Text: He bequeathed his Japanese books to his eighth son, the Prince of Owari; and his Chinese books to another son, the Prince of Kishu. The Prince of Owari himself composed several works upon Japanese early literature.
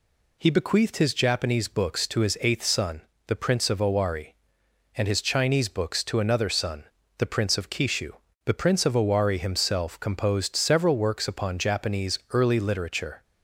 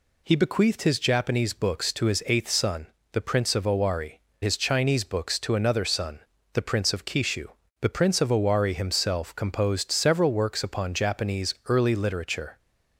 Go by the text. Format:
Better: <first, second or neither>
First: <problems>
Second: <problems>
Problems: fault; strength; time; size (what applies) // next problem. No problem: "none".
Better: first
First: none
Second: skips "and"; at 4.3 s